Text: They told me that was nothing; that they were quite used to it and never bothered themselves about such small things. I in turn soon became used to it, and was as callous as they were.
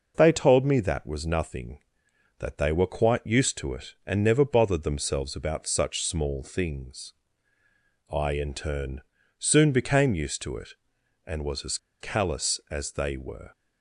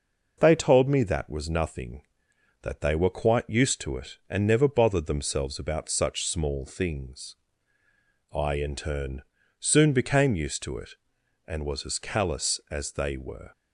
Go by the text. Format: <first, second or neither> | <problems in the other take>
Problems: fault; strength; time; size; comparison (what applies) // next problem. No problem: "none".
second | pauses between "turn" and "soon"; at 9.0 s; 0.38 s long; also in the second // pauses between "as" and "callous"; slight; at 11.7 s; 0.23 s long